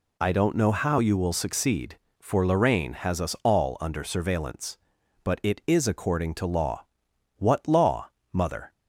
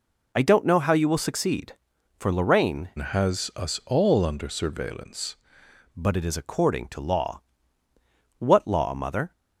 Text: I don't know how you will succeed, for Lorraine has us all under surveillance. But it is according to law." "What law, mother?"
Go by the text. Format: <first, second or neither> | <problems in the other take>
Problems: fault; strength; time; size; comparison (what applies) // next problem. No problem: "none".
first | changes voice from "has" to "surveillance"; from 2.9 to 5.3 s; 2.4 s long